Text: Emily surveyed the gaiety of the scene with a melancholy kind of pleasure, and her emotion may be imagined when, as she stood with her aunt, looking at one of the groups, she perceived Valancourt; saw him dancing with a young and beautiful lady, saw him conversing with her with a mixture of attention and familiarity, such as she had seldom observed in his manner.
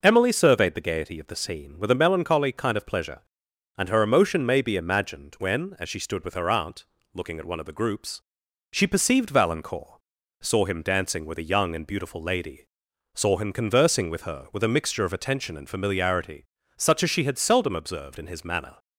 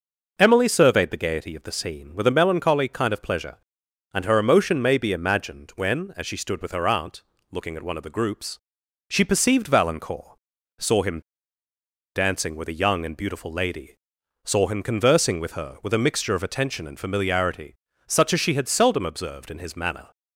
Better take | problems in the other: first | pauses between "him" and "dancing"; noticeable; at 11.1 s; 0.95 s long

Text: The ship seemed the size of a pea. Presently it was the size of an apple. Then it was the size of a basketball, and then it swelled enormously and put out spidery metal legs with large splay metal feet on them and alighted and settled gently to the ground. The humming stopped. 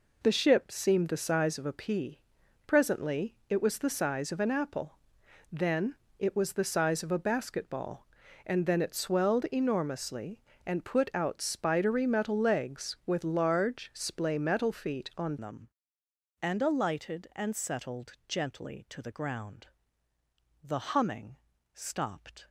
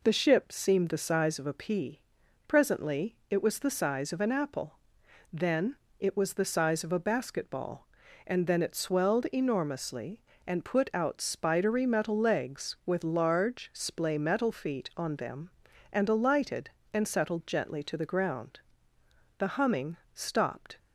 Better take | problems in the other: second | pauses between "Then" and "it"; slight; at 5.9 s; 0.22 s long; slight in the second // changes voice at "them"; from 15.4 s on; 7.0 s long // pauses between "humming" and "stopped"; slight; at 21.3 s; 0.36 s long; slight in the second

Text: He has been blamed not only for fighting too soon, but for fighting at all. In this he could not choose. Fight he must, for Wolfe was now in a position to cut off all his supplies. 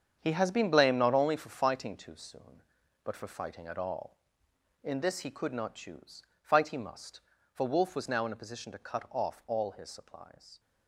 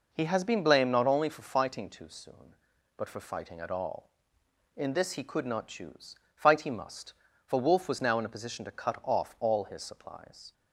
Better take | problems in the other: second | gets quieter; strong; throughout; 10 dB

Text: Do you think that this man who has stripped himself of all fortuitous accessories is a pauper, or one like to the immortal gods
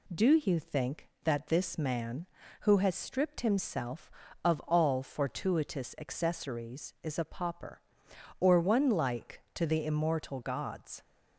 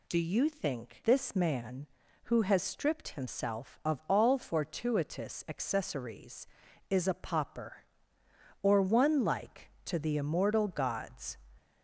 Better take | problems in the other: first | skips "that"; at 1.0 s

